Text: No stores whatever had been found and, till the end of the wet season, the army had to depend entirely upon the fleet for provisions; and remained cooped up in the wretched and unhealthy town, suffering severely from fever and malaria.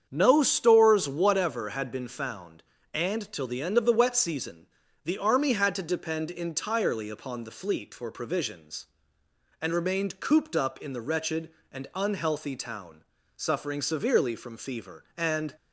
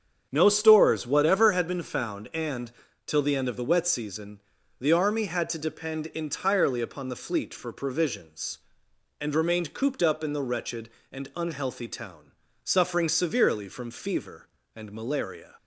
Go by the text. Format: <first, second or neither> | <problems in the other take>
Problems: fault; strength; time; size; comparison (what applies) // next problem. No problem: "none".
second | starts louder than the rest; strong; until 1.1 s; 7.5 dB; strong in the second // stops before "malaria"; at 15.5 s